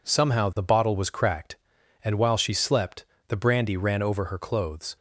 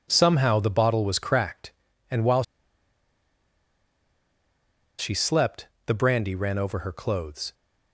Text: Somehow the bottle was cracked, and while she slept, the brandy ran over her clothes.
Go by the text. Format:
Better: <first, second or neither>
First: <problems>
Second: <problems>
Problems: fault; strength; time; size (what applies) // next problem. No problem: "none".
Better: first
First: none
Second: pauses between "while" and "she"; strong; at 2.4 s; 2.5 s long